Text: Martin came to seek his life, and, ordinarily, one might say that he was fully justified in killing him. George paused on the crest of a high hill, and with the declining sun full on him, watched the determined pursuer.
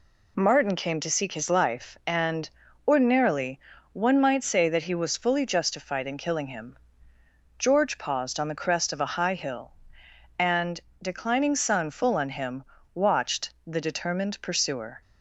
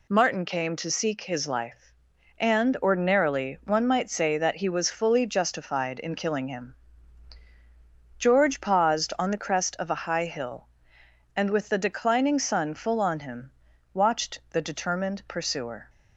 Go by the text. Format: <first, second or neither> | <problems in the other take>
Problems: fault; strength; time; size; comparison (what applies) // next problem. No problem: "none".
second | skips "with the"; at 10.9 s